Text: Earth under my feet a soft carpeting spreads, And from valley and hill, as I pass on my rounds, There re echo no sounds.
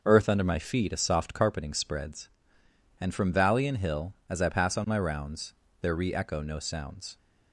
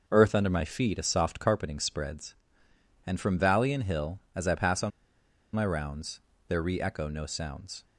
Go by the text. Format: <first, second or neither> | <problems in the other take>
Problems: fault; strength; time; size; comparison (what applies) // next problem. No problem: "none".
first | pauses between "on" and "my"; noticeable; at 4.9 s; 0.65 s long